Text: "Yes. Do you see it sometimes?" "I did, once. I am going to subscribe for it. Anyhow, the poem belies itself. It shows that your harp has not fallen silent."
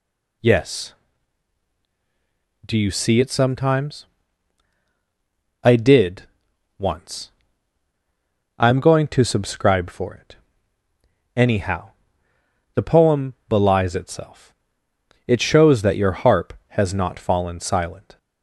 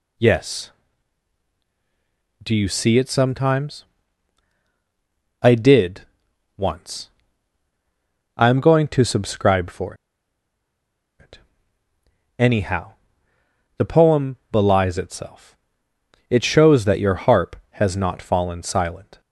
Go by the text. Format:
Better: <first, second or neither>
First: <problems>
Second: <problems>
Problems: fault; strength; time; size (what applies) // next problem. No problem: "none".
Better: first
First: pauses between "poem" and "belies"; slight; at 13.3 s; 0.16 s long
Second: pauses between "for" and "it"; strong; at 9.9 s; 1.2 s long // pauses between "poem" and "belies"; slight; at 14.3 s; 0.16 s long